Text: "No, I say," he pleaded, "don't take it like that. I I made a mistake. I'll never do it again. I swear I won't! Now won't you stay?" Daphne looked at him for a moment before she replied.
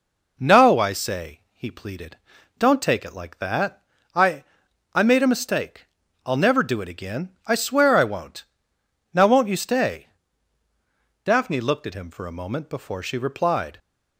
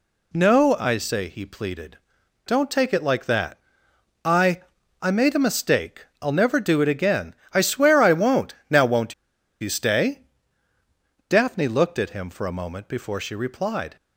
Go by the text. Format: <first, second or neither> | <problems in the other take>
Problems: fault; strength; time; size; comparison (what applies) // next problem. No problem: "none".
first | pauses between "I" and "I"; at 4.6 s; 0.40 s long; noticeable in the first // pauses between "won't" and "you"; noticeable; at 9.1 s; 0.47 s long